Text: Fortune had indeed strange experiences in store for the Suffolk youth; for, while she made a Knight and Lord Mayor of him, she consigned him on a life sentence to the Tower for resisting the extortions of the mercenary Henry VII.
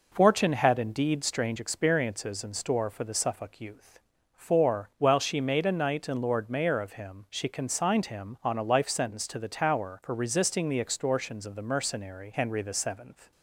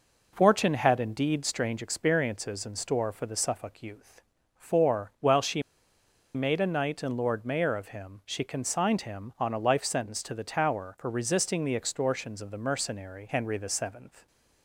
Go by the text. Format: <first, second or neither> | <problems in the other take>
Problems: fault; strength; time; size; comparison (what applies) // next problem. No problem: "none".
first | pauses between "she" and "made"; noticeable; at 5.6 s; 0.72 s long